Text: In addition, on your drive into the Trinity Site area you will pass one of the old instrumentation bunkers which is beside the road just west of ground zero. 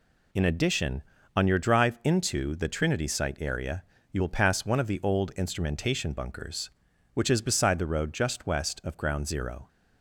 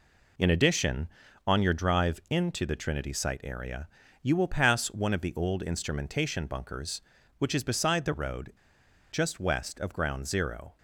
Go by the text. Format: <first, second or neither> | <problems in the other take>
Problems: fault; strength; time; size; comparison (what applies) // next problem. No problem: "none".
first | pauses between "area" and "you"; at 3.8 s; 0.38 s long; slight in the first // pauses between "road" and "just"; noticeable; at 8.5 s; 0.58 s long